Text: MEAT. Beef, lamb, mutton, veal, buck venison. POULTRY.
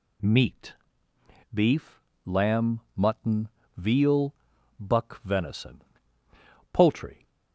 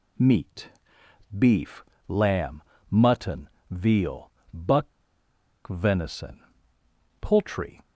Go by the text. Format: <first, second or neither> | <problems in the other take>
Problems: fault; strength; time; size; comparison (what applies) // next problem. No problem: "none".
first | pauses between "buck" and "venison"; noticeable; at 4.8 s; 0.77 s long